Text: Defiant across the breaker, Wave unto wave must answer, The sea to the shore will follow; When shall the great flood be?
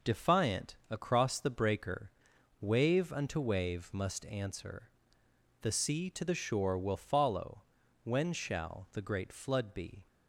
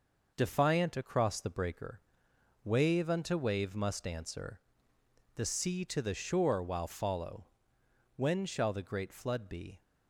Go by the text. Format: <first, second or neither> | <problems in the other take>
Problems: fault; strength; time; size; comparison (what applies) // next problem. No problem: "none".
first | says "while" for "will"; at 6.6 s